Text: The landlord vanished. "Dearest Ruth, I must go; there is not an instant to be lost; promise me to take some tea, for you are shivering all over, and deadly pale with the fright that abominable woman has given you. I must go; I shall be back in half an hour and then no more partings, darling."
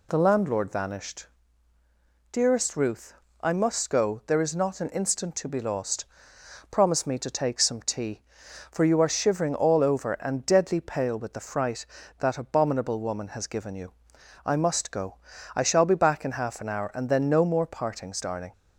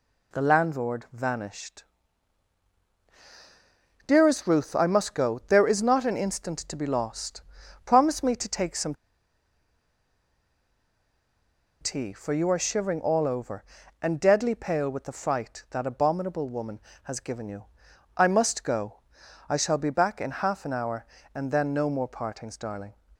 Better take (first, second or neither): first